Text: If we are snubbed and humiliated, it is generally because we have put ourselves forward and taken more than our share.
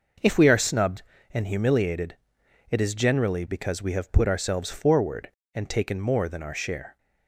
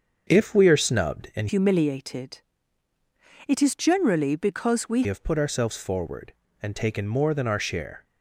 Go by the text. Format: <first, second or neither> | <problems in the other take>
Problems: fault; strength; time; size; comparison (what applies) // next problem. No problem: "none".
first | starts louder than the rest; until 1.2 s; 7 dB // changes voice from "humiliated" to "we"; from 1.4 to 5.0 s; 3.6 s long